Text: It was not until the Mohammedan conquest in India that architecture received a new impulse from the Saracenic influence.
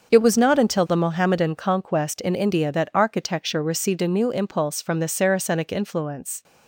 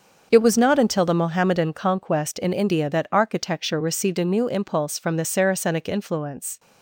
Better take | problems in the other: neither | starts louder than the rest; the same in both

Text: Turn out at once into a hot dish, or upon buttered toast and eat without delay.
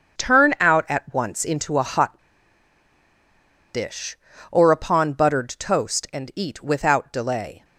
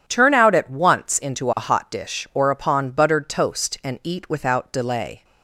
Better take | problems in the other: second | starts louder than the rest; until 1.2 s; 6.5 dB // pauses between "hot" and "dish"; strong; at 2.1 s; 1.5 s long

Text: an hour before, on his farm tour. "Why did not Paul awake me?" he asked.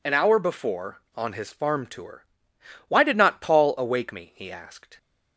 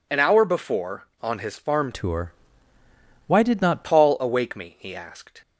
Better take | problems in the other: first | changes voice from "tour" to "not"; from 1.9 to 3.8 s; 1.9 s long

